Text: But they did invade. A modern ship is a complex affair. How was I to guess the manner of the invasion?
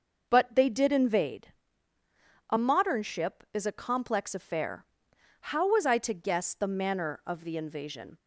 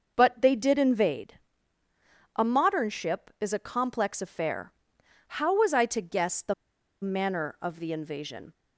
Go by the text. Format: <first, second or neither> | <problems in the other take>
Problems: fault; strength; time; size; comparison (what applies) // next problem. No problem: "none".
first | starts louder than the rest; noticeable; until 1.1 s; 6 dB; noticeable in the first // pauses between "the" and "manner"; noticeable; at 6.5 s; 0.49 s long